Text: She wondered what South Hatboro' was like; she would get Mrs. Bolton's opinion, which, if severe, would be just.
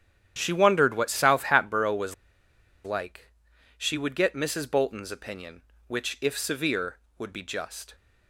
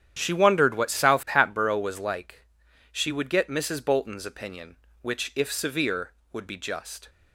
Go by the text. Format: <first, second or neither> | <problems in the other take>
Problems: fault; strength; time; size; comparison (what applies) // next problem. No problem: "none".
second | starts louder than the rest; strong; until 1.3 s; 9.5 dB; strong in the second // pauses between "was" and "like"; noticeable; at 2.1 s; 0.71 s long